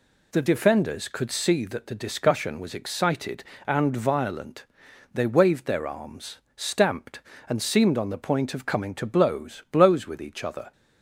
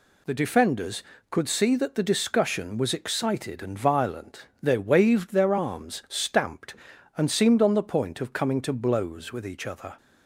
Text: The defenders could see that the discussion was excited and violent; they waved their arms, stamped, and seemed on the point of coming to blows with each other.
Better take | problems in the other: second | says "blows" twice; at 9.6 s

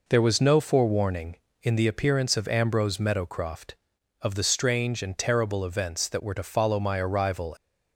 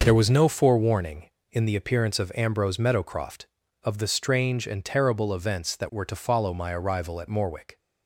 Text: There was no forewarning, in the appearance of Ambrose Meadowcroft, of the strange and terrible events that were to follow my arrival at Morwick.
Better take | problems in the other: second | stops before "at Morwick"; at 7.5 s

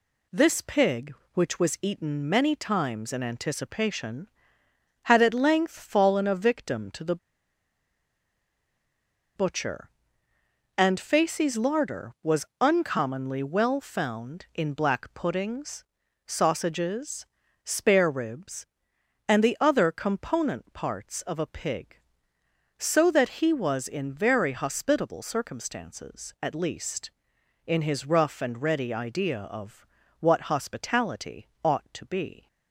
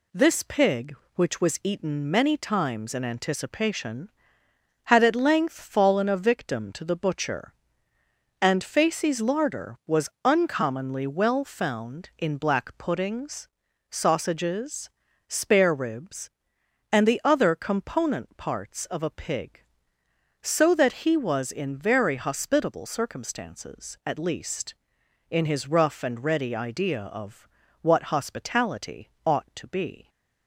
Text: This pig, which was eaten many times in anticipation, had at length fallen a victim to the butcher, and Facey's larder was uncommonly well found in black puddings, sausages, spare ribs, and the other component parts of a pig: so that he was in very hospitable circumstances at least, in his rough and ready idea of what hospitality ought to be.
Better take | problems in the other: second | pauses between "the" and "butcher"; strong; at 7.1 s; 2.1 s long // pauses between "was" and "uncommonly"; slight; at 12.4 s; 0.16 s long; slight in the second // pauses between "of" and "what"; slight; at 29.8 s; 0.32 s long; slight in the second // pauses between "hospitality" and "ought"; slight; at 31.4 s; 0.16 s long; slight in the second

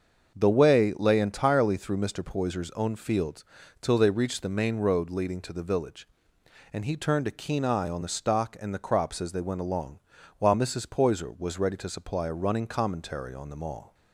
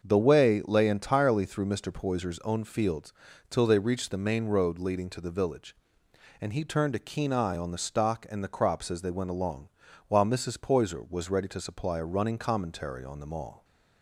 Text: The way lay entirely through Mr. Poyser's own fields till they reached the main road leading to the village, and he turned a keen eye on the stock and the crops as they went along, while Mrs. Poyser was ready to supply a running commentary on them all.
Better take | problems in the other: neither | starts louder than the rest; the same in both // pauses between "fields" and "till"; the same in both

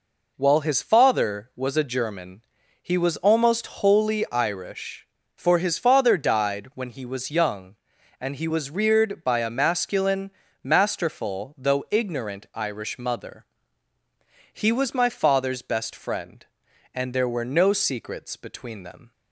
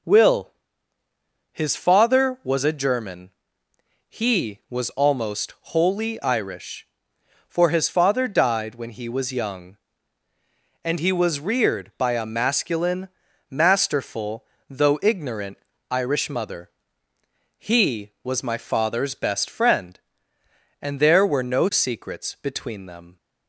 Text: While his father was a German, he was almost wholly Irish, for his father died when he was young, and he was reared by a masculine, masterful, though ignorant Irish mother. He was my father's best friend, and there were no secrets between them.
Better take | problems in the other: first | says "Will" for "While"; at 0.0 s // pauses between "ignorant" and "Irish"; slight; at 15.5 s; 0.32 s long

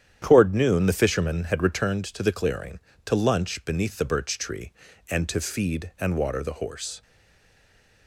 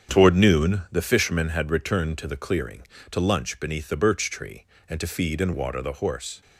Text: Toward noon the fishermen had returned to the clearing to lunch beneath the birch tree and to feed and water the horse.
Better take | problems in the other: second | starts louder than the rest; strong; until 1.2 s; 9.5 dB; strong in the second // stays silent after the last word; from 7.0 s on; 1.0 s long

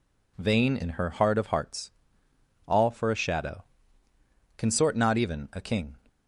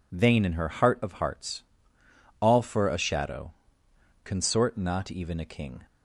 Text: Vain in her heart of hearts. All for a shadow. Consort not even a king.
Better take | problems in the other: neither | none

